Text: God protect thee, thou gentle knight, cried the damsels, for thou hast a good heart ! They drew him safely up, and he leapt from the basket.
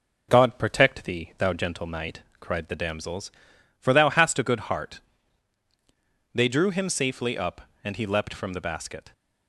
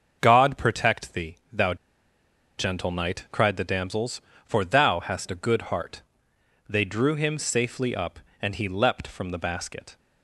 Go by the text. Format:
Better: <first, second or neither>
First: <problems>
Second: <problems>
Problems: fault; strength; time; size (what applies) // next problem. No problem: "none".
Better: first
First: none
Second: starts louder than the rest; until 1.2 s; 6.5 dB // pauses between "thou" and "gentle"; noticeable; at 1.7 s; 0.82 s long